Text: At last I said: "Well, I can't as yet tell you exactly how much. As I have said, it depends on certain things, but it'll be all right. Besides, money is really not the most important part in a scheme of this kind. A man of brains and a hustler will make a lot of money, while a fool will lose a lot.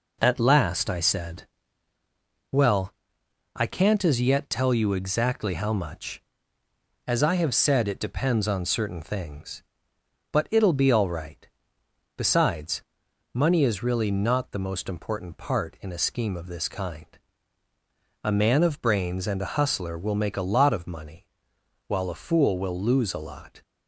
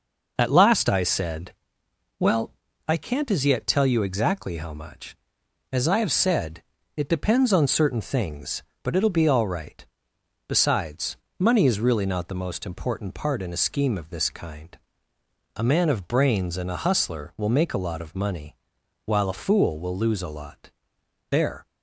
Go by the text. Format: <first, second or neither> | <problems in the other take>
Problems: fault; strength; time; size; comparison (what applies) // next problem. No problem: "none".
first | goes on to say "There"; slight; from 21.2 s on; 0.36 s long